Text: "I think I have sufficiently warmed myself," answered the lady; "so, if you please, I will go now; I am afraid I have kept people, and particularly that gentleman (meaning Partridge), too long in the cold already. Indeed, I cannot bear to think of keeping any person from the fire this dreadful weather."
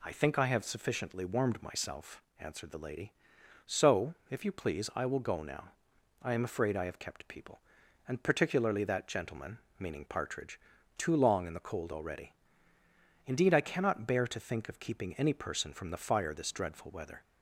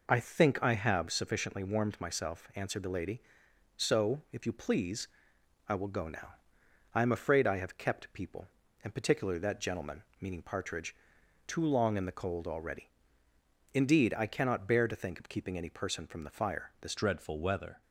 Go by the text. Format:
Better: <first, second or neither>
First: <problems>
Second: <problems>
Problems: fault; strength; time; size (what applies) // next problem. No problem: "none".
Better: first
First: none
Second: changes voice at "dreadful"; from 16.9 s on; 0.9 s long